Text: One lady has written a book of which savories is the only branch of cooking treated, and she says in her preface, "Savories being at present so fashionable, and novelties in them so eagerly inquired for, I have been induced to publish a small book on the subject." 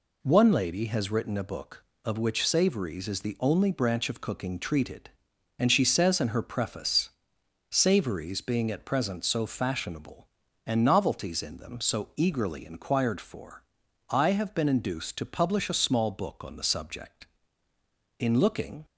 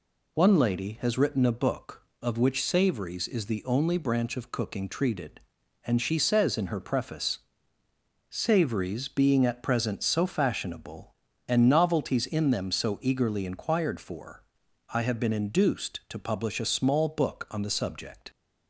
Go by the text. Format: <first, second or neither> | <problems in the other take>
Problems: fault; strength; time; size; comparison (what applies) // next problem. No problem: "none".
second | goes on to say "In looking"; noticeable; from 18.1 s on; 0.66 s long